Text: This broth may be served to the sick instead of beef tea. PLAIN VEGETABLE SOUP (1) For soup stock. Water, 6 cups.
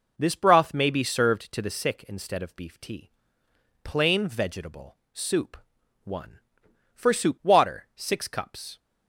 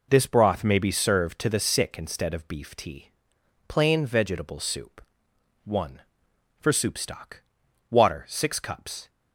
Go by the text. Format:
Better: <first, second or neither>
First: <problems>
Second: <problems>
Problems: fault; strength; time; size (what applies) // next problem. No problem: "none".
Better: second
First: pauses between "VEGETABLE" and "SOUP"; slight; at 4.9 s; 0.16 s long // skips "stock"; at 7.4 s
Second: none